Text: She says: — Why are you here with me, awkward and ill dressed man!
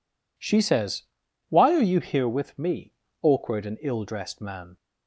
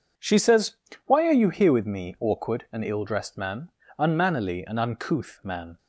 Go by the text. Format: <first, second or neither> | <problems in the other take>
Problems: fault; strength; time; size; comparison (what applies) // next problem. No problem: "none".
first | goes on to say "Unmannerly and uncouth man"; strong; from 3.9 s on; 1.7 s long